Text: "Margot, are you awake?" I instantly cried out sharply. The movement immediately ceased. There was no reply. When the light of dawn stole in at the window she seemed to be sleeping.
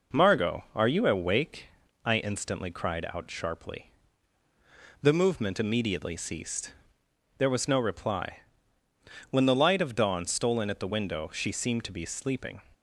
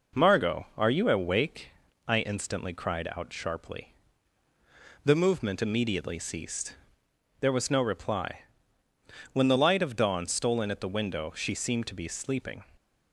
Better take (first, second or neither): neither